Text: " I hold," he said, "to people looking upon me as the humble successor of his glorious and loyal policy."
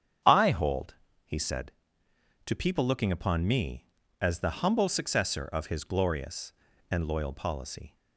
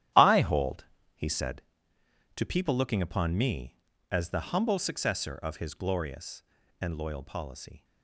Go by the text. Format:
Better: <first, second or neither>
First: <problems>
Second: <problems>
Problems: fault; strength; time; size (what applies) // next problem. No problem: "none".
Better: first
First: starts louder than the rest; strong; until 1.5 s; 8.5 dB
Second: gets quieter; strong; throughout; 12 dB // starts louder than the rest; strong; until 1.4 s; 12 dB